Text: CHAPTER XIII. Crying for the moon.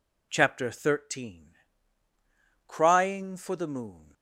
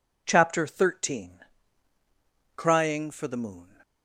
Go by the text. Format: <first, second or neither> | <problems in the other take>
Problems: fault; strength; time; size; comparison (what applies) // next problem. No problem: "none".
neither | none